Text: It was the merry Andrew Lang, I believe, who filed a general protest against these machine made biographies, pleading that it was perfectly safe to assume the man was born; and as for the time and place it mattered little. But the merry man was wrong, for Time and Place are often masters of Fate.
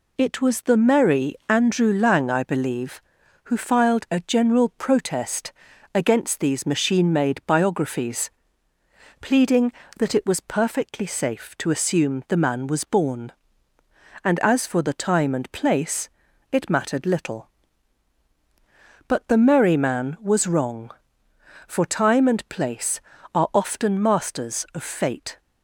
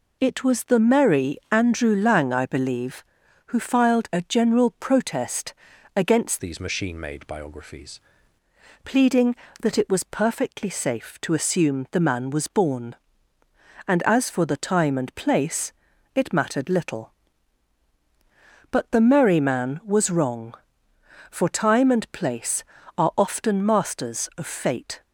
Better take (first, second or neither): first